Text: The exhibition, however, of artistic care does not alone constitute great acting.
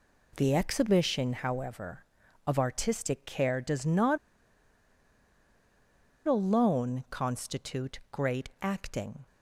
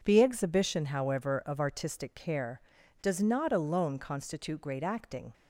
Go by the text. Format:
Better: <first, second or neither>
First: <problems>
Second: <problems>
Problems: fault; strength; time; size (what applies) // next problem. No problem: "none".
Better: second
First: pauses between "not" and "alone"; strong; at 4.1 s; 2.0 s long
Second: none